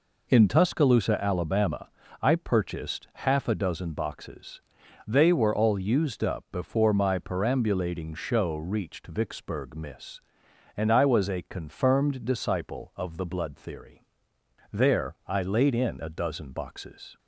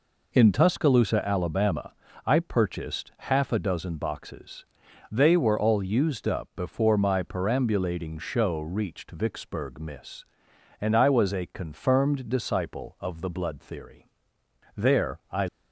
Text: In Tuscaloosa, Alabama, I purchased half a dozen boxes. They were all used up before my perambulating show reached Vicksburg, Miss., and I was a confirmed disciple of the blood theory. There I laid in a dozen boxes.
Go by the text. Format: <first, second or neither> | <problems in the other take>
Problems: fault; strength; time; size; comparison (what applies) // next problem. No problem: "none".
first | stops before "laid in a dozen boxes"; at 15.4 s